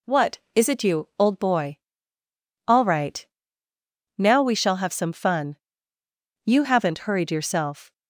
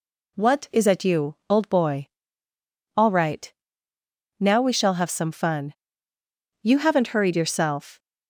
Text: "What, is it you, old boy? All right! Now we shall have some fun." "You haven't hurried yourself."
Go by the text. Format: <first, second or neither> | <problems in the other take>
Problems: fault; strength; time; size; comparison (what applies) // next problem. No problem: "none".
first | says "at" for "it"; at 0.8 s